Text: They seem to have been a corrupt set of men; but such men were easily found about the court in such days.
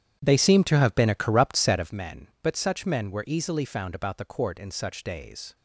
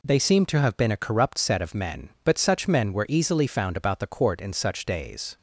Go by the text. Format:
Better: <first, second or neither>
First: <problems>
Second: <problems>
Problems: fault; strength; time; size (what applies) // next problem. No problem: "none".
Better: second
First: starts louder than the rest; strong; until 1.9 s; 10 dB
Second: none